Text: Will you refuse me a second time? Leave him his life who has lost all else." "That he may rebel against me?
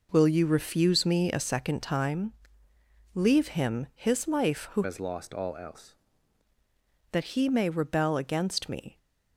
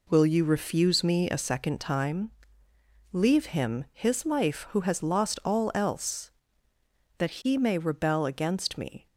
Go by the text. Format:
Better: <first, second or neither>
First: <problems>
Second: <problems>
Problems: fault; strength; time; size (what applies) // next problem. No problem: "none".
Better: second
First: changes voice from "has" to "else"; from 4.8 to 5.9 s; 1.1 s long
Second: none